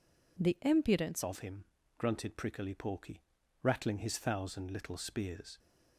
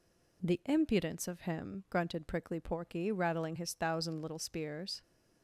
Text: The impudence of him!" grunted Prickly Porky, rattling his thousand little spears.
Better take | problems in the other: second | changes voice at "of"; from 1.2 s on; 4.3 s long

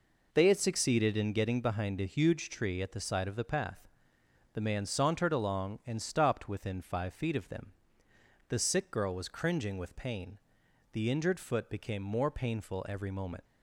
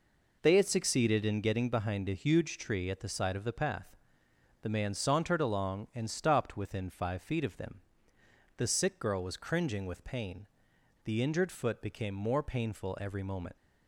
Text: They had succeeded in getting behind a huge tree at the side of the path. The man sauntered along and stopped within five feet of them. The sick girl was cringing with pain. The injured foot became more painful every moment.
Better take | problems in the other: neither | none

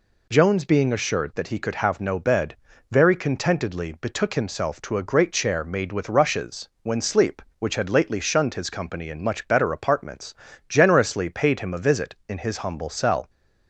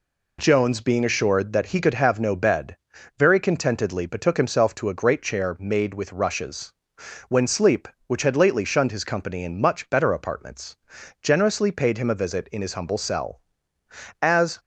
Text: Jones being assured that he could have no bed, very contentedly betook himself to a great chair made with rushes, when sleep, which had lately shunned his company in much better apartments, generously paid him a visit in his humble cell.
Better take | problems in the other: first | goes on to say "As"; slight; from 14.2 s on; 0.38 s long

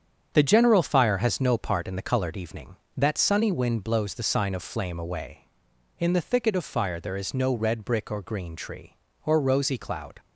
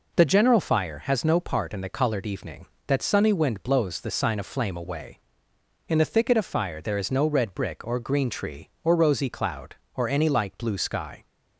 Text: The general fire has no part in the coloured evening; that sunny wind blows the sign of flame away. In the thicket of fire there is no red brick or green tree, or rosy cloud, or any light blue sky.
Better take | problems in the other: second | starts louder than the rest; strong; until 1.3 s; 8 dB // stops before "or any light blue sky"; at 10.1 s

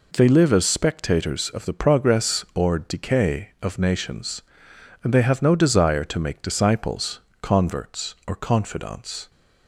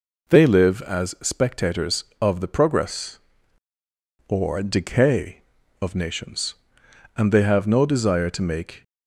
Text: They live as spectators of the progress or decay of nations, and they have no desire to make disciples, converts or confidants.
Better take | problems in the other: first | stops before "disciples converts or confidants"; at 8.8 s

